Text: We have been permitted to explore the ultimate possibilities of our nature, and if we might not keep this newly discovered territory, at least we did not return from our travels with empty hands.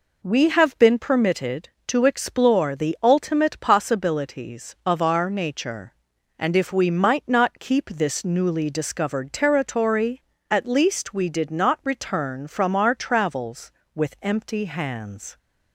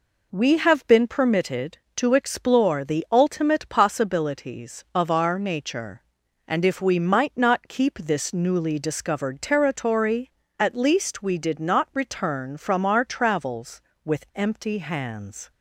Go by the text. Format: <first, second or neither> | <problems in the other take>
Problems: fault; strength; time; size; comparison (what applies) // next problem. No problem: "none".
neither | none